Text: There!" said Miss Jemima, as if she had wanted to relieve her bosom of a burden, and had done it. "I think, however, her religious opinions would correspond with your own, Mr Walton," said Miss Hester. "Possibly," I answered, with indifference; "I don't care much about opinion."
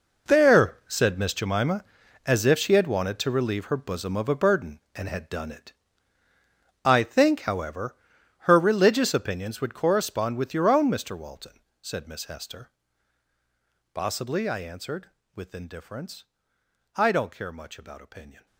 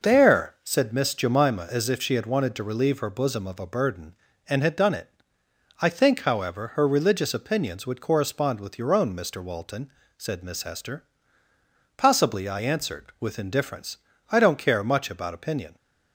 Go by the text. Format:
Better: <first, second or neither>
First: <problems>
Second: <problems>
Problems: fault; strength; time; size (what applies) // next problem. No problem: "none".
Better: second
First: gets quieter; strong; throughout; 14.5 dB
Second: none